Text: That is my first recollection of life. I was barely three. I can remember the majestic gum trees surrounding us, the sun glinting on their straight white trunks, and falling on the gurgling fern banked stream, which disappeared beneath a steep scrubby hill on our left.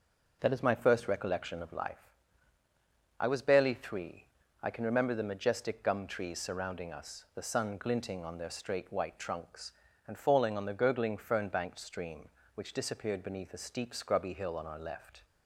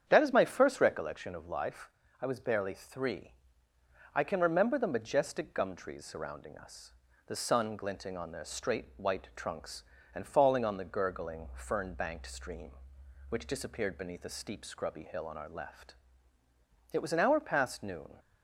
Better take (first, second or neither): first